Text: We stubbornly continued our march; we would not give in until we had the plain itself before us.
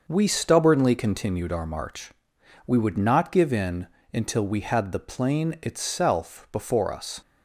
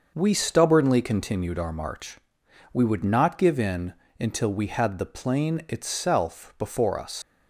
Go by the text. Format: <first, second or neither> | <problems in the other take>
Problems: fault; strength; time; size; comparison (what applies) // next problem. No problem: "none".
first | starts louder than the rest; noticeable; until 1.1 s; 6 dB; also in the first // pauses between "in" and "until"; slight; at 3.9 s; 0.26 s long; slight in the first // leaves "us" unfinished; at 7.2 s; 50 ms